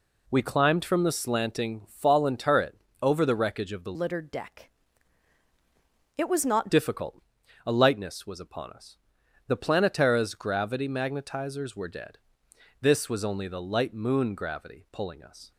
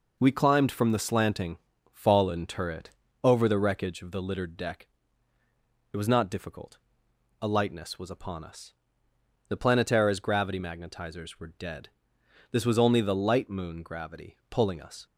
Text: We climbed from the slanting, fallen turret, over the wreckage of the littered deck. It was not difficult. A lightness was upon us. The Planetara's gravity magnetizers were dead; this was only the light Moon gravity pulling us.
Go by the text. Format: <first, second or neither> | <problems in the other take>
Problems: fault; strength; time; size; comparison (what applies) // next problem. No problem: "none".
second | changes voice from "littered" to "not"; from 3.9 to 6.6 s; 2.7 s long